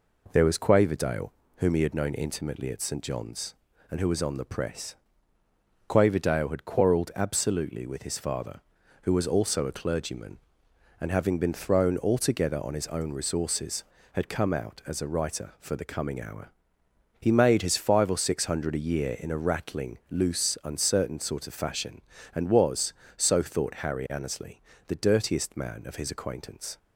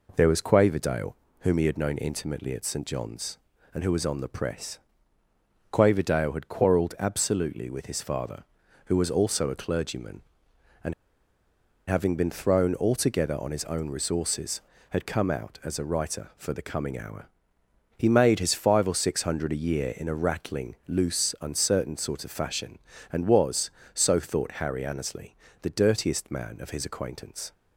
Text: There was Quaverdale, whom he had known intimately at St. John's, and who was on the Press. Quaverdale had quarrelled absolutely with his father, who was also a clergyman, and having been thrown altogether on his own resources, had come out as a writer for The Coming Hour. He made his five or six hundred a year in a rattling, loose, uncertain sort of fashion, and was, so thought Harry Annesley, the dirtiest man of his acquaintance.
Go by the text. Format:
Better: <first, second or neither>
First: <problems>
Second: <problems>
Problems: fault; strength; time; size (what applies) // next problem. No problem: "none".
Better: first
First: none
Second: pauses between "and" and "having"; noticeable; at 10.9 s; 0.96 s long